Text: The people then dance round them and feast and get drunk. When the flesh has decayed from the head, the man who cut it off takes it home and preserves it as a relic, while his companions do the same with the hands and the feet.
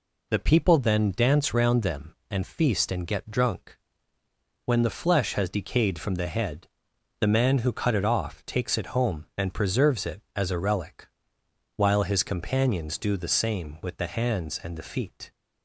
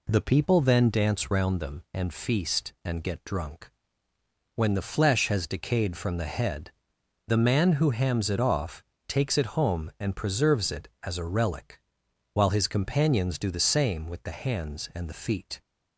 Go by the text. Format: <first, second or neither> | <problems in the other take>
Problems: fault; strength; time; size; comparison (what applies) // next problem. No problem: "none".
first | says "hams" for "cut"; at 7.9 s // pauses between "off" and "takes"; slight; at 8.8 s; 0.24 s long